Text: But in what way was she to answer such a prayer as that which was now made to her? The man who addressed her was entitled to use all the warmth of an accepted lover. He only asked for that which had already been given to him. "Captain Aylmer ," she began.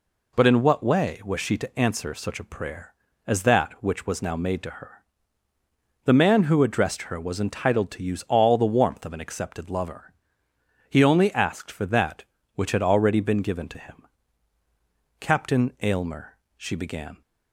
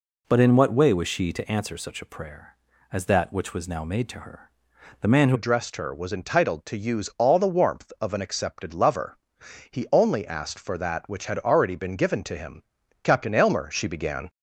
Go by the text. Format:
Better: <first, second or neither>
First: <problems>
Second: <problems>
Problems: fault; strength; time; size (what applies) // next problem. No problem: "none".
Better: first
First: none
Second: changes voice at "addressed"; from 5.3 s on; 8.9 s long